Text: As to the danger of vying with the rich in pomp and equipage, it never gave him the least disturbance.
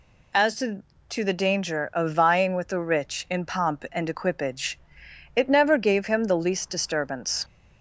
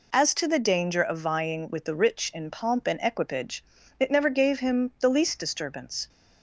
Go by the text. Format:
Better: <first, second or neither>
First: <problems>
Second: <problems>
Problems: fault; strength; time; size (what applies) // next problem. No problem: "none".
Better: second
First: says "to" twice; at 1.1 s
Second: none